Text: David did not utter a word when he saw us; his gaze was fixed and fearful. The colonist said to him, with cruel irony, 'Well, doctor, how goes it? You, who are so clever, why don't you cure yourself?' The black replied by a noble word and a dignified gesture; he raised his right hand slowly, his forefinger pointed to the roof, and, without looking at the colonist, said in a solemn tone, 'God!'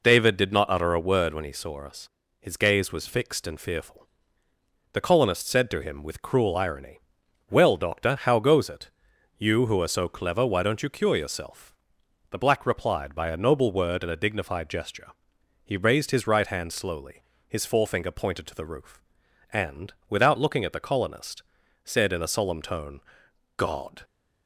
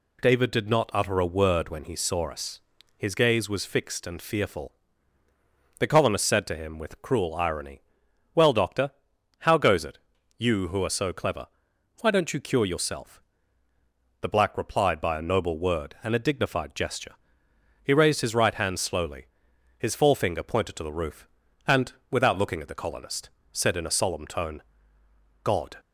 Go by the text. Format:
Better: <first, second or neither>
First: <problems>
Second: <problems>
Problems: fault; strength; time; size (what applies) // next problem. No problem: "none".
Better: neither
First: none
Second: none